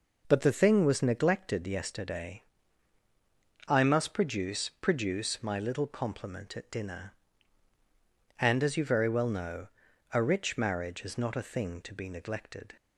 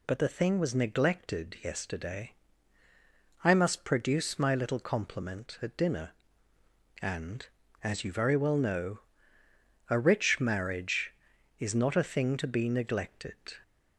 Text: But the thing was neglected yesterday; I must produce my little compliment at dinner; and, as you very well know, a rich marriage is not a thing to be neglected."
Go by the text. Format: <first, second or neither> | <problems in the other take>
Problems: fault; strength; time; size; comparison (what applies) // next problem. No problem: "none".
second | says "produce" twice; at 4.8 s